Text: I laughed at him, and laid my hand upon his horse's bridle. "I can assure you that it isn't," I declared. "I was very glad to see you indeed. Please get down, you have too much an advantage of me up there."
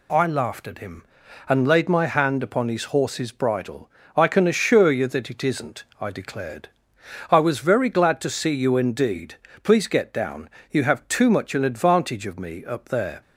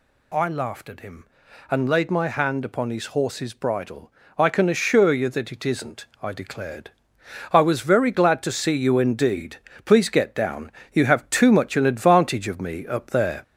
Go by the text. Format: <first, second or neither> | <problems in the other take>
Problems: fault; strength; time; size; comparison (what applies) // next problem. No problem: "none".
first | gets louder; throughout; 3.5 dB